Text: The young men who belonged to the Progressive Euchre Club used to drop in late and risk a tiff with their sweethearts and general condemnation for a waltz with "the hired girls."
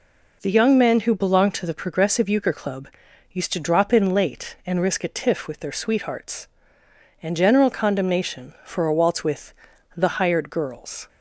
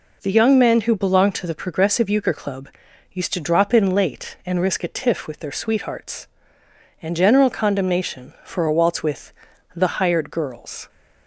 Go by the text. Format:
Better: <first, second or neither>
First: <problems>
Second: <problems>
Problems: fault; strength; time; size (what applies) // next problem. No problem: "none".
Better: neither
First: pauses between "Club" and "used"; noticeable; at 2.8 s; 0.46 s long // pauses between "with" and "the"; at 9.5 s; 0.44 s long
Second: pauses between "Club" and "used"; noticeable; at 2.6 s; 0.46 s long // pauses between "with" and "the"; at 9.3 s; 0.44 s long